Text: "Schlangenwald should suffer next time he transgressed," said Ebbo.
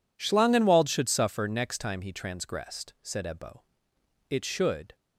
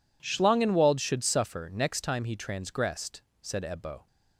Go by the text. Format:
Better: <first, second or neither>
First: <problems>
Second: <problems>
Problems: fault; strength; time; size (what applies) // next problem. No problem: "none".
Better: second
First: goes on to say "It should"; noticeable; from 4.2 s on; 0.66 s long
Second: none